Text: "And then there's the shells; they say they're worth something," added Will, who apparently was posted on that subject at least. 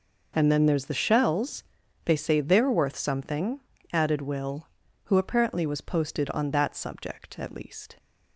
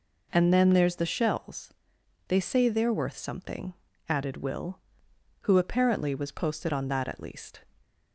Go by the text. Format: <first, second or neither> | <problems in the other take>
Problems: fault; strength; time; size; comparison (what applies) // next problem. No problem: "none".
first | skips "subject"; at 7.0 s